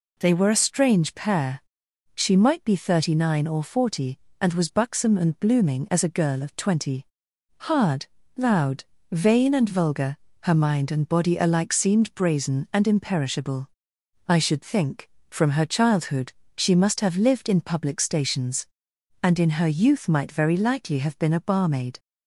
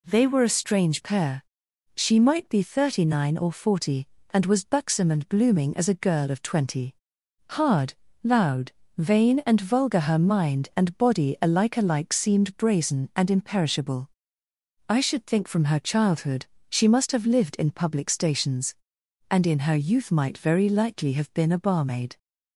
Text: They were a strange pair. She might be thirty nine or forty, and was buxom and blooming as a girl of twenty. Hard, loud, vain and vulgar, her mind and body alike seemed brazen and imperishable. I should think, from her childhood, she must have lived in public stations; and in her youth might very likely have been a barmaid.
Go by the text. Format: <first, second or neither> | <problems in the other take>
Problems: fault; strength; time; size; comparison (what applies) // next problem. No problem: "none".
first | says "alike" twice; at 11.7 s